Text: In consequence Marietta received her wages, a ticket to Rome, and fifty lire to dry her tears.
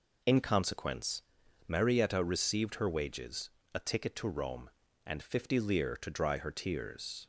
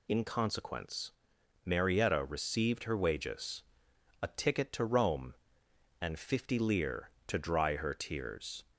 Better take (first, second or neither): second